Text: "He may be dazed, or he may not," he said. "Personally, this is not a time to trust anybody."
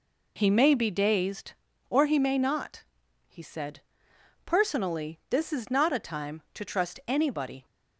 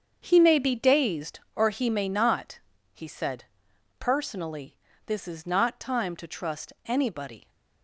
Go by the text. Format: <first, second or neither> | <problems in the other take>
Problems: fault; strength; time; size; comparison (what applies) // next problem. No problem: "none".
first | starts louder than the rest; strong; until 1.2 s; 7 dB // skips "a"; at 5.8 s